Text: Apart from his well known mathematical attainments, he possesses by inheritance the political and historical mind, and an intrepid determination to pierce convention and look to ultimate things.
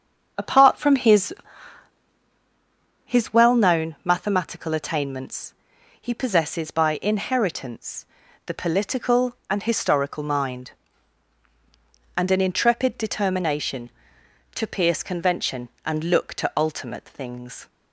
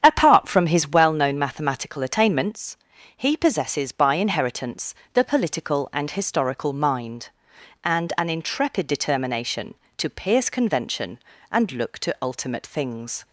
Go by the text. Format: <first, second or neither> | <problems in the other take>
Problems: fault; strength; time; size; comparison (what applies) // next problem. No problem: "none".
second | starts louder than the rest; strong; until 3.0 s; 7 dB; strong in the second // says "his" twice; at 3.0 s // pauses between "inheritance" and "the"; at 8.0 s; 0.40 s long; slight in the second